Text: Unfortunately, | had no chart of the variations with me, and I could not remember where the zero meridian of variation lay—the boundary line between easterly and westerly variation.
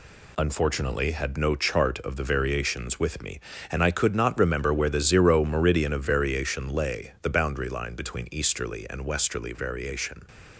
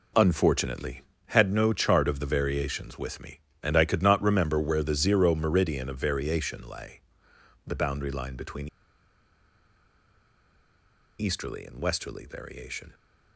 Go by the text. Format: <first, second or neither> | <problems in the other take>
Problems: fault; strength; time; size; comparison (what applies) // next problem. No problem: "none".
first | pauses between "between" and "easterly"; strong; at 8.6 s; 2.5 s long